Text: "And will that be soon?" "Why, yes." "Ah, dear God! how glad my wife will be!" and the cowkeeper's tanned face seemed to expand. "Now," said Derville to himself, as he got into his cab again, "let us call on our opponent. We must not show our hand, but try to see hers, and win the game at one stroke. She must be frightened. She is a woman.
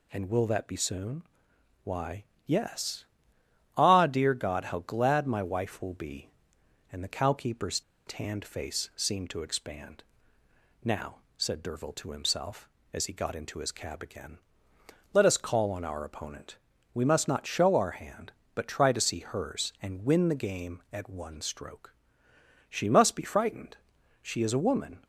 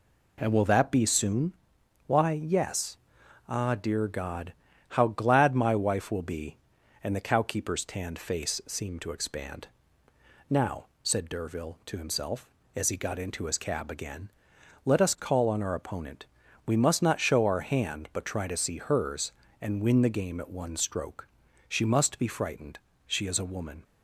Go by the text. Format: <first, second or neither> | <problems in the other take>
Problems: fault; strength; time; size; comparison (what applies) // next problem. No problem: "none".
second | pauses between "cowkeeper's" and "tanned"; slight; at 7.7 s; 0.27 s long